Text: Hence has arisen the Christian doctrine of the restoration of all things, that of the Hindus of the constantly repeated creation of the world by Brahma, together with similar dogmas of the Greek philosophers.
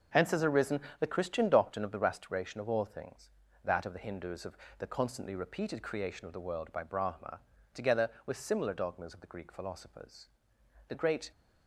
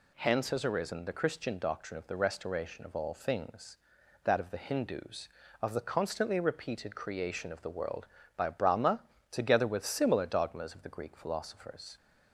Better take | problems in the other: second | starts louder than the rest; noticeable; until 1.3 s; 6 dB // pauses between "arisen" and "the"; slight; at 0.8 s; 0.20 s long // pauses between "of" and "the"; slight; at 4.5 s; 0.18 s long // goes on to say "The great"; slight; from 10.8 s on; 0.42 s long

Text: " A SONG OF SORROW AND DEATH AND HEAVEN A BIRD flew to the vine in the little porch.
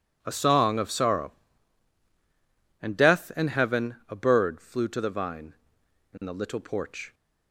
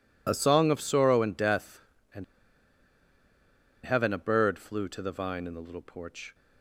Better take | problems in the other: first | pauses between "AND" and "HEAVEN"; strong; at 2.2 s; 1.5 s long

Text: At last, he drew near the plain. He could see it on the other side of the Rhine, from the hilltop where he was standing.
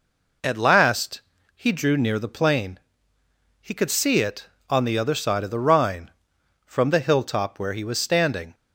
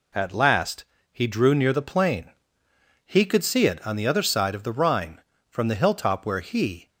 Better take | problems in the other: first | stops before "was standing"; at 6.8 s

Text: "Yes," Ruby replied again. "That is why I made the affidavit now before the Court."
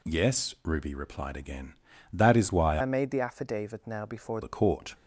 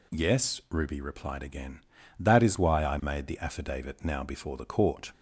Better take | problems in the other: second | changes voice from "I" to "before"; from 2.7 to 4.3 s; 1.6 s long

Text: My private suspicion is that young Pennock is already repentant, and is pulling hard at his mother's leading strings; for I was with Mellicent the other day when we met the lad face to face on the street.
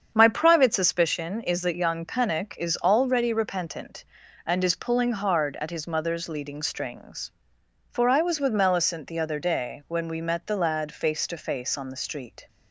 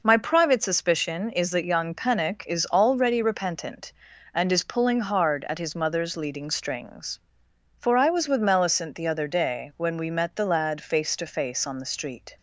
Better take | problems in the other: second | starts louder than the rest; strong; until 1.0 s; 7.5 dB

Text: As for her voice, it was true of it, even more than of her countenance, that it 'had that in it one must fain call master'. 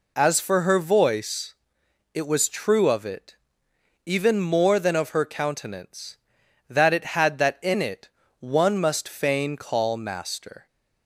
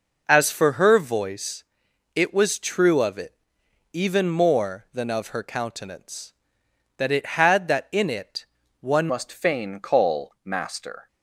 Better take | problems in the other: first | pauses between "it" and "one"; slight; at 8.4 s; 0.34 s long; slight in the first // changes voice at "must"; from 9.0 s on; 2.0 s long

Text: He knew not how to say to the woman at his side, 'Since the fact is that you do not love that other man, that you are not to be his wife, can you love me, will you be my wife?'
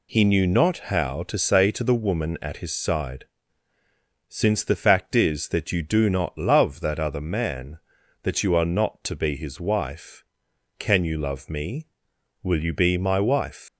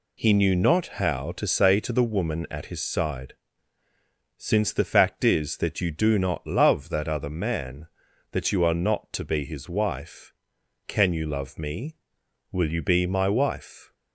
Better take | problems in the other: second | leaves "wife" unfinished; at 13.6 s; 155 ms

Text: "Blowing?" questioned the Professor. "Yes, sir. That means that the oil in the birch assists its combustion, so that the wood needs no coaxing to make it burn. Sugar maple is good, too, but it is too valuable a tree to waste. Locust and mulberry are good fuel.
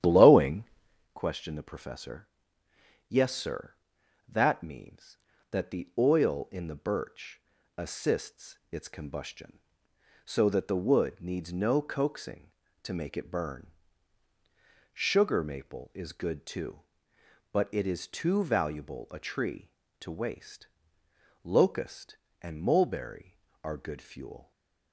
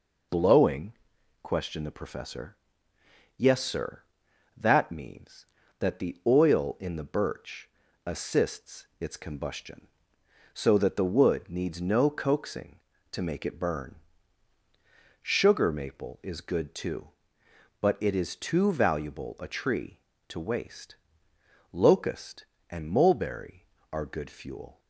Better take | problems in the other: second | starts louder than the rest; strong; until 1.2 s; 10.5 dB // pauses between "birch" and "assists"; at 7.3 s; 0.38 s long; also in the second // stays silent after the last word; slight; from 24.4 s on; 0.5 s long

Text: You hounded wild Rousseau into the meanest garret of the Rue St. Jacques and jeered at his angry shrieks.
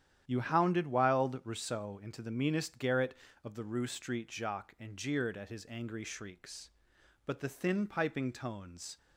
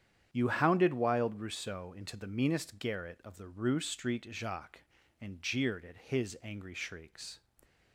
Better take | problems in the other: second | starts louder than the rest; strong; until 1.2 s; 10.5 dB; strong in the second // goes on to say "But the thin piping tones"; strong; from 7.2 s on; 1.7 s long

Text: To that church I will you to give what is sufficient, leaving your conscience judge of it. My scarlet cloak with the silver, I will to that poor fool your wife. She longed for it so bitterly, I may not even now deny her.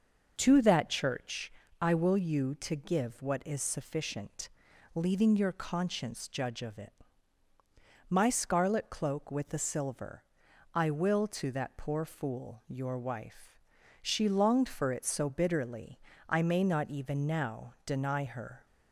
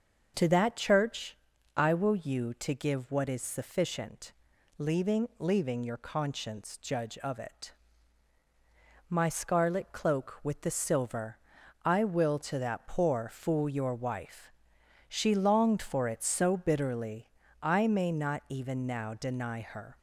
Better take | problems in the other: first | starts louder than the rest; until 1.3 s; 6.5 dB // pauses between "church" and "I"; at 1.3 s; 0.40 s long; slight in the first // says "leaving" twice; at 5.3 s

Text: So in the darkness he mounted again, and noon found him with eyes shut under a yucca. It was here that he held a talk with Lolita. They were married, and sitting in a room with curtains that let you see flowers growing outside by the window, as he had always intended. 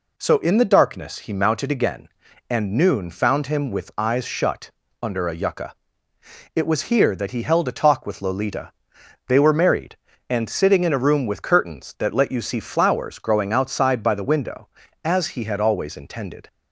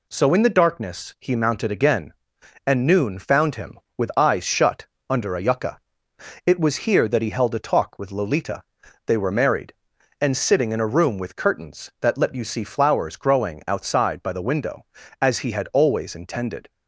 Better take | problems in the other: neither | pauses between "shut" and "under"; slight; the same in both

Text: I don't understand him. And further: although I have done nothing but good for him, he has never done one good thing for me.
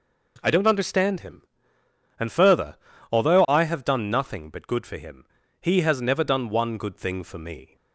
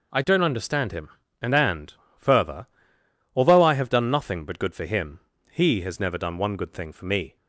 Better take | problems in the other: first | says "And" twice; at 1.5 s

